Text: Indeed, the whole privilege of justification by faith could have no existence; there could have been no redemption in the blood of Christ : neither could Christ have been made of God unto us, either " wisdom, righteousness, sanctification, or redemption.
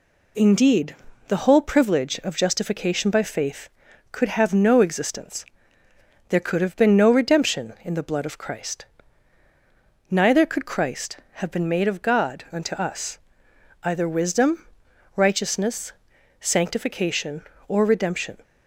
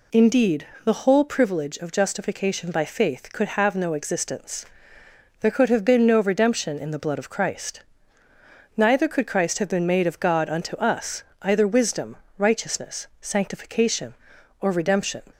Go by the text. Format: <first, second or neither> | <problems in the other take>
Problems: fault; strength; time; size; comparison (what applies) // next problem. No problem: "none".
neither | none